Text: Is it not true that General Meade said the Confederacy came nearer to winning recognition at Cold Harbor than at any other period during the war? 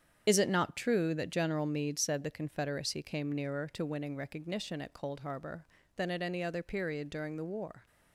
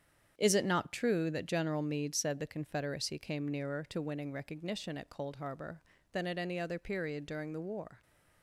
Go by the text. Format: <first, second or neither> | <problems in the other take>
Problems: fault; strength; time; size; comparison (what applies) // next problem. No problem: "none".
second | loses the start of "Is"; at 0.2 s; 55 ms // starts louder than the rest; strong; until 1.2 s; 8 dB; strong in the second